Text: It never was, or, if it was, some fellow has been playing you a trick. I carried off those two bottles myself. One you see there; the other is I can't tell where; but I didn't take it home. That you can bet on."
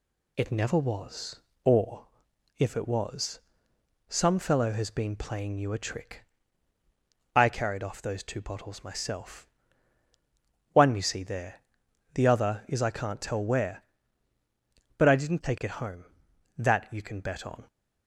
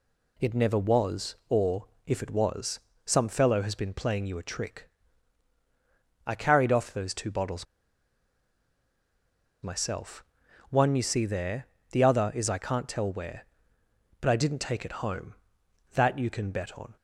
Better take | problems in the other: first | pauses between "bottles" and "myself"; strong; at 7.6 s; 1.9 s long

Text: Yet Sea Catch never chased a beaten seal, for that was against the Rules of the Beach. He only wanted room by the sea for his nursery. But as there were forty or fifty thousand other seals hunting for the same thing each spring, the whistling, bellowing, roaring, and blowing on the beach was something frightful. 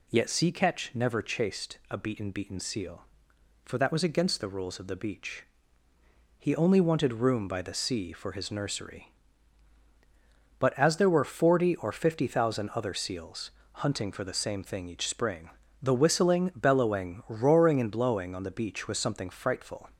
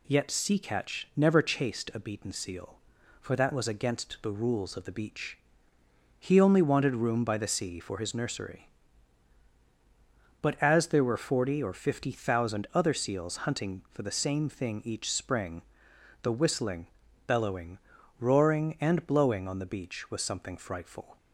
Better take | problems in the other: second | says "beaten" twice; at 2.3 s // pauses between "seals" and "hunting"; slight; at 13.5 s; 0.22 s long

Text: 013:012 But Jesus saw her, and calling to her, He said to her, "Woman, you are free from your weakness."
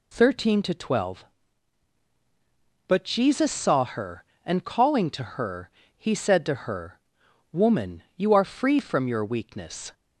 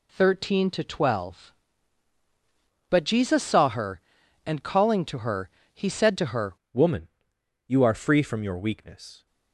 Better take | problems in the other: first | changes voice at "Woman"; from 6.7 s on; 2.5 s long

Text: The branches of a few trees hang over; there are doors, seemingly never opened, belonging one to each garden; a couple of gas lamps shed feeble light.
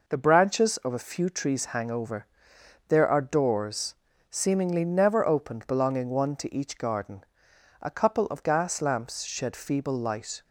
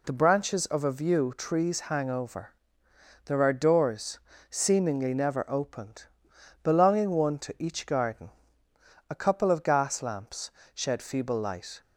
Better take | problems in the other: first | says "view" for "few"; at 0.9 s // pauses between "lamps" and "shed"; slight; at 10.5 s; 0.24 s long

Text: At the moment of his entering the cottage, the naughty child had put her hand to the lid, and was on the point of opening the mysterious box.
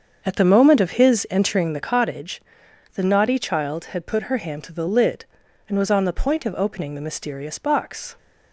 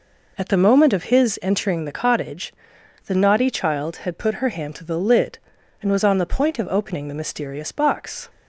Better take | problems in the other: second | starts louder than the rest; until 2.0 s; 7 dB

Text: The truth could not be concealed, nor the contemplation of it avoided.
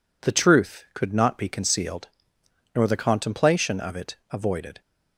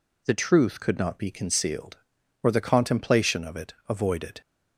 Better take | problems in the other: first | says "or" for "nor"; at 2.4 s // pauses between "it" and "avoided"; slight; at 3.7 s; 0.16 s long

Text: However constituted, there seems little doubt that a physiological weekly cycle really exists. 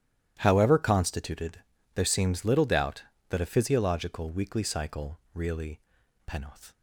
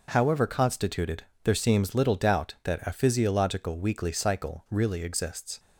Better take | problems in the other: second | starts louder than the rest; strong; until 1.3 s; 12 dB // pauses between "cycle" and "really"; slight; at 5.1 s; 0.16 s long // says "penoth" for "exists"; at 6.2 s

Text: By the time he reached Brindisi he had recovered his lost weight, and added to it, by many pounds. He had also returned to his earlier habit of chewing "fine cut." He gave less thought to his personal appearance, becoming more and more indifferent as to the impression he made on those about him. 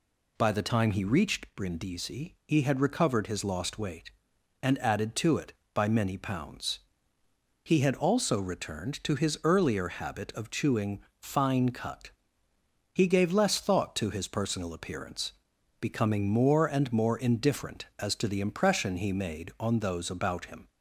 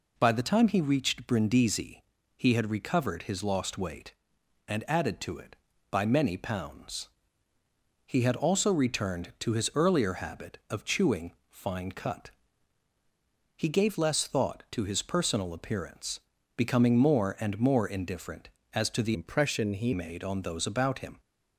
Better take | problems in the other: first | pauses between "Brindisi" and "he"; slight; at 2.0 s; 0.36 s long // pauses between "chewing" and "fine"; slight; at 11.3 s; 0.18 s long; slight in the first // changes voice from "impression" to "he"; from 19.1 to 19.9 s; 0.8 s long

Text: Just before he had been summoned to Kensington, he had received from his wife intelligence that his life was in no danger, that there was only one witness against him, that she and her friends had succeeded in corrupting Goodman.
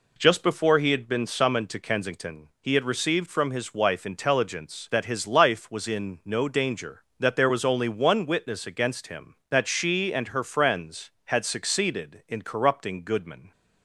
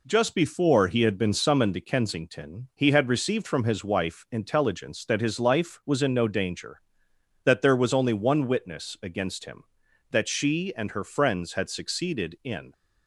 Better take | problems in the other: first | stops before "corrupting Goodman"; at 12.7 s

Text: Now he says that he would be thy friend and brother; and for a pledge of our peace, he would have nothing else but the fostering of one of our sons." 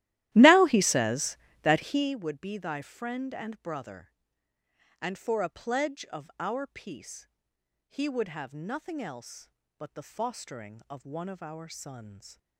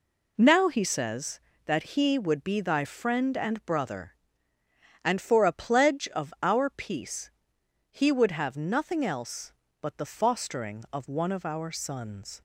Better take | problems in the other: second | starts louder than the rest; strong; until 2.1 s; 14.5 dB

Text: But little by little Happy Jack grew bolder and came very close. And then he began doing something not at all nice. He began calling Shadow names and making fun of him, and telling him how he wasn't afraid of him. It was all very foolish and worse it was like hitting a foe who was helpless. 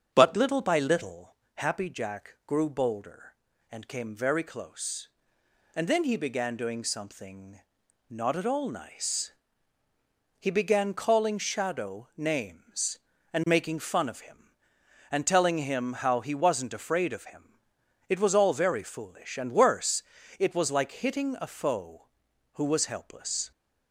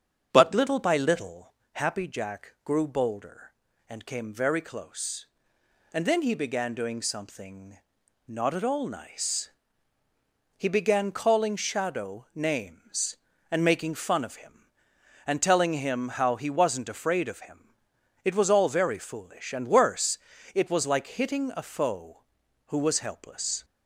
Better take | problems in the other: neither | starts louder than the rest; strong; the same in both // pauses between "little" and "Happy"; slight; the same in both // pauses between "something" and "not"; noticeable; the same in both // pauses between "worse" and "it"; slight; the same in both

